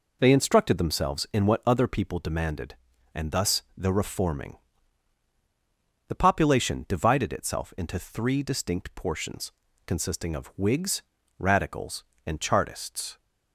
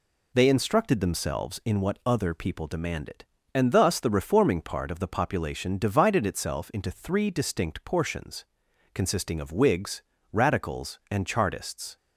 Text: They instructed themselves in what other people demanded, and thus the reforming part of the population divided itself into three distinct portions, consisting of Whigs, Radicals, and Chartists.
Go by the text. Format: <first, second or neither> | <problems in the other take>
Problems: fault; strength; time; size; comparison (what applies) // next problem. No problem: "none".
second | skips "part of"; at 5.3 s